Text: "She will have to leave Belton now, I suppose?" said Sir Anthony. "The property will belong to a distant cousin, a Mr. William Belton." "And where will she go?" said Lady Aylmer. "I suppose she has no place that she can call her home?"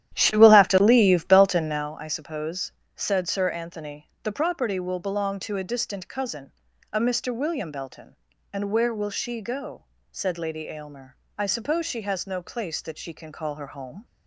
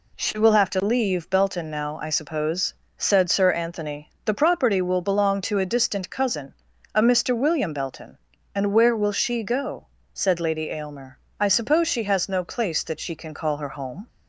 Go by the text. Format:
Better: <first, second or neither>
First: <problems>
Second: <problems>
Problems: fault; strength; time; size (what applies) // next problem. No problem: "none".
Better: second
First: starts louder than the rest; strong; until 2.0 s; 11.5 dB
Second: none